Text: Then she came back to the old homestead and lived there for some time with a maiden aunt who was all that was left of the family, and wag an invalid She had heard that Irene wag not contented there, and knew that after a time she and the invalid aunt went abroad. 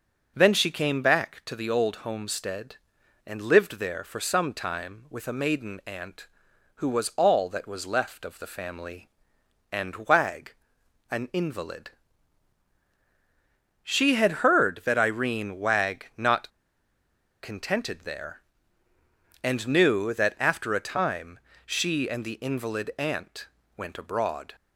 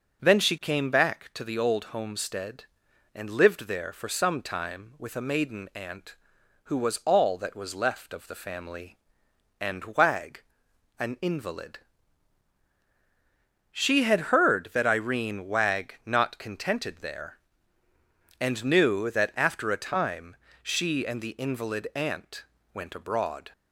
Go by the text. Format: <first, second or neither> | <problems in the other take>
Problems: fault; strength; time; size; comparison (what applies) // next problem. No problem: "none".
second | pauses between "wag" and "an"; noticeable; at 10.5 s; 0.56 s long; noticeable in the second // pauses between "invalid" and "She"; strong; at 11.9 s; 1.9 s long; strong in the second // pauses between "not" and "contented"; noticeable; at 16.4 s; 0.92 s long // pauses between "time" and "she"; slight; at 21.3 s; 0.26 s long; slight in the second // pauses between "aunt" and "went"; slight; at 23.4 s; 0.30 s long; slight in the second